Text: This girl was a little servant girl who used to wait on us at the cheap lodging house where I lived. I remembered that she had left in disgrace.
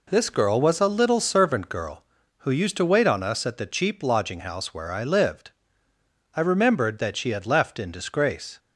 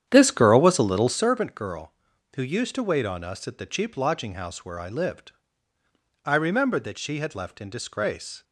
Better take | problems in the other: first | starts louder than the rest; strong; until 1.3 s; 9.5 dB

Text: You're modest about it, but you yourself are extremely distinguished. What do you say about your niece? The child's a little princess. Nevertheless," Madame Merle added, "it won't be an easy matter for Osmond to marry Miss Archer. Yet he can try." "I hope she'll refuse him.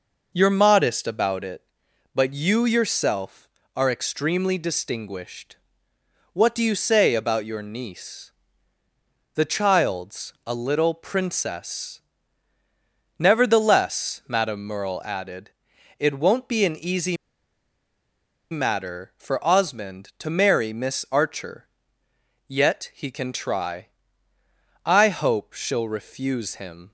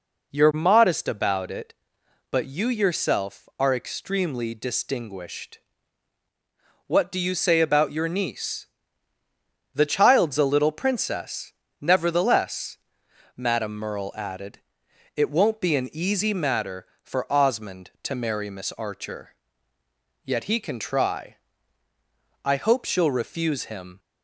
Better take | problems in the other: second | pauses between "easy" and "matter"; strong; at 17.1 s; 1.3 s long

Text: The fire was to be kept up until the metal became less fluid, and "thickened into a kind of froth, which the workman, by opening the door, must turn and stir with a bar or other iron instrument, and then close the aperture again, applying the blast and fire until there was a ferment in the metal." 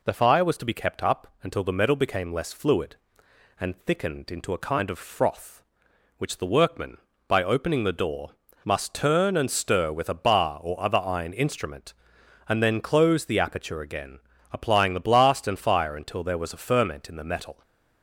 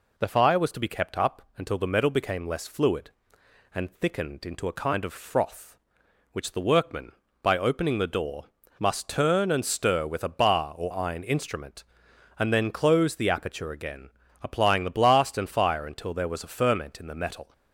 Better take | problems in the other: first | pauses between "up" and "until"; slight; at 1.4 s; 0.16 s long; slight in the first // skips "other"; at 10.9 s

